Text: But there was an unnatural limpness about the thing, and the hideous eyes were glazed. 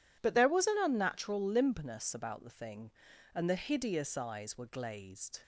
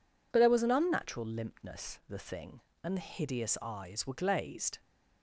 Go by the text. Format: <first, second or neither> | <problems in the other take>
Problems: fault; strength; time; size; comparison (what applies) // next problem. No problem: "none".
first | skips "about"; at 2.0 s